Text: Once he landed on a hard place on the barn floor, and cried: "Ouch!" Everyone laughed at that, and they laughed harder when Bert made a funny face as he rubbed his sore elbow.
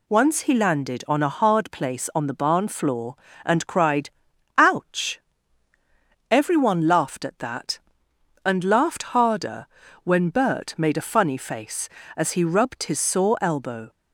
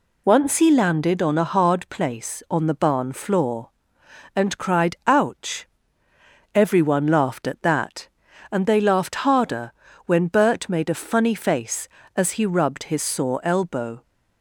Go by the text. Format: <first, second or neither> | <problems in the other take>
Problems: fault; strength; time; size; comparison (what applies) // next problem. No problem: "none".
second | skips "they"; at 8.6 s // pauses between "harder" and "when"; at 9.6 s; 0.38 s long; slight in the second